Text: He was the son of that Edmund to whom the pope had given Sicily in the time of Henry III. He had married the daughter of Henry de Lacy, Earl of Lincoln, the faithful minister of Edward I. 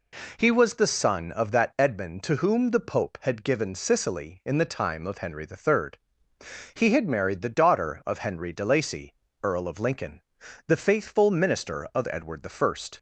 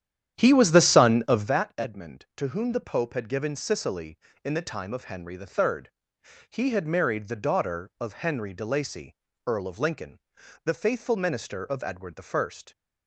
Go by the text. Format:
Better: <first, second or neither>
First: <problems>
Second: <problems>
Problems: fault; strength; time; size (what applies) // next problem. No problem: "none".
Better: first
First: none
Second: starts louder than the rest; strong; until 1.6 s; 10 dB